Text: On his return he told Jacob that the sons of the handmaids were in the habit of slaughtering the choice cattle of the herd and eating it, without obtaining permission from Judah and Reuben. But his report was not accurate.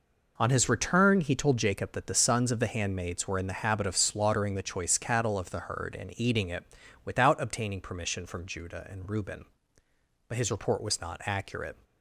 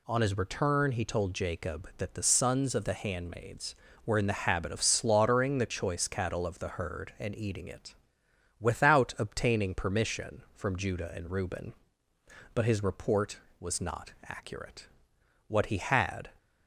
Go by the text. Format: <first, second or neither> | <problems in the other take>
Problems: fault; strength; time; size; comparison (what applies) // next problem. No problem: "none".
first | goes on to say "What he had"; noticeable; from 15.4 s on; 0.82 s long